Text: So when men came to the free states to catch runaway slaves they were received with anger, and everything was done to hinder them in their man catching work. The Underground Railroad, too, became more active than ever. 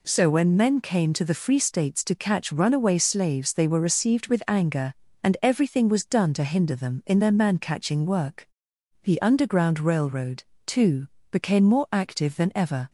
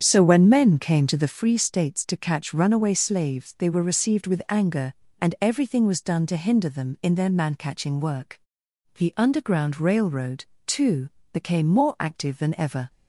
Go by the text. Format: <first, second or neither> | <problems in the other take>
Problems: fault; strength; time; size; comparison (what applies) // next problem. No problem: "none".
first | starts louder than the rest; strong; until 1.4 s; 8 dB